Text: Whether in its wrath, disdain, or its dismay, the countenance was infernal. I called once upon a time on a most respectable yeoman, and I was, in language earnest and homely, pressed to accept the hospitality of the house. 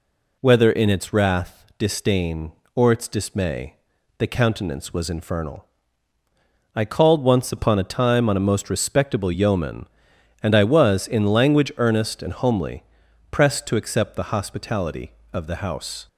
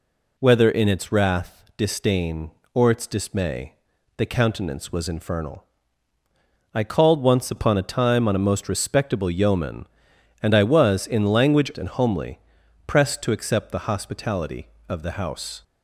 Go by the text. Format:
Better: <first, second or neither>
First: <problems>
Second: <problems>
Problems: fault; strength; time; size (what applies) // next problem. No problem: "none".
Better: first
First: none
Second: skips "earnest"; at 11.7 s